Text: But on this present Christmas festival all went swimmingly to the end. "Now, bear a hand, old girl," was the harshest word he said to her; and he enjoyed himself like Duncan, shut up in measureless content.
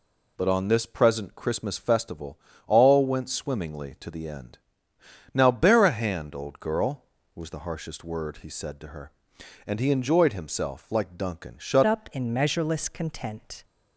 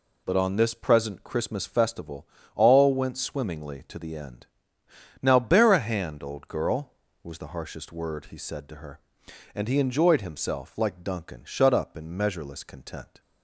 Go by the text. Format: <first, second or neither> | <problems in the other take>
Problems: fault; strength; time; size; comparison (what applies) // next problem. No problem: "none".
second | pauses between "festival" and "all"; slight; at 2.3 s; 0.28 s long; slight in the second // changes voice at "up"; from 11.8 s on; 1.8 s long